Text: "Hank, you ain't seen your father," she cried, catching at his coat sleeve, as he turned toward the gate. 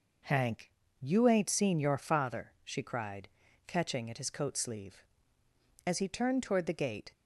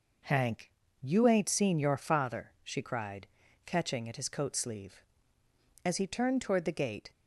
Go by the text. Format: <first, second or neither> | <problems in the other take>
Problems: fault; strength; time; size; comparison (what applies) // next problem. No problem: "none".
neither | none